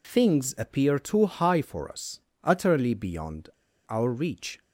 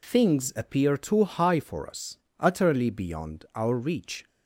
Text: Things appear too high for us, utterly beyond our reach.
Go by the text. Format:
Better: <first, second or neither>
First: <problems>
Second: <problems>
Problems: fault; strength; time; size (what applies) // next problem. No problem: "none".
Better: second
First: pauses between "beyond" and "our"; at 3.4 s; 0.38 s long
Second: none